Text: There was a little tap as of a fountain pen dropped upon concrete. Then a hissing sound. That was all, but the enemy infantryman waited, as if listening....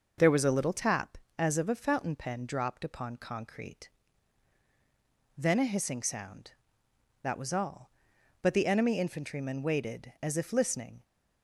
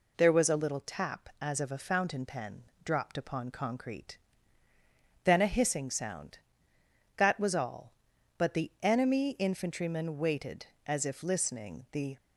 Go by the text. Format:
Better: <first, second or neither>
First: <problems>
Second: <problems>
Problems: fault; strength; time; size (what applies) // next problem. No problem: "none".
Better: first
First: none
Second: pauses between "pen" and "dropped"; slight; at 2.6 s; 0.22 s long // goes on to say "The"; slight; from 11.9 s on; 0.24 s long